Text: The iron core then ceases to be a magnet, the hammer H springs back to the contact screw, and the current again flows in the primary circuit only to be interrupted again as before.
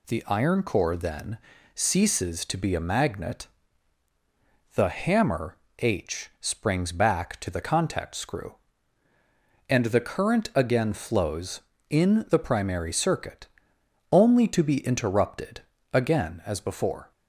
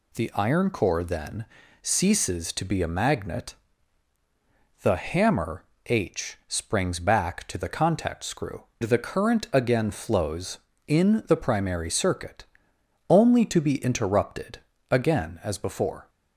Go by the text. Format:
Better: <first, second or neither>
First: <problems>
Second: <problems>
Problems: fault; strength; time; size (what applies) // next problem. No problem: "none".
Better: first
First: pauses between "then" and "ceases"; slight; at 1.3 s; 0.36 s long // pauses between "hammer" and "H"; slight; at 5.5 s; 0.22 s long // pauses between "circuit" and "only"; noticeable; at 13.4 s; 0.64 s long // pauses between "interrupted" and "again"; slight; at 15.6 s; 0.32 s long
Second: pauses between "then" and "ceases"; slight; at 1.4 s; 0.36 s long // pauses between "hammer" and "H"; slight; at 5.6 s; 0.22 s long // skips "and"; at 8.7 s // pauses between "circuit" and "only"; noticeable; at 12.4 s; 0.64 s long // pauses between "interrupted" and "again"; slight; at 14.5 s; 0.32 s long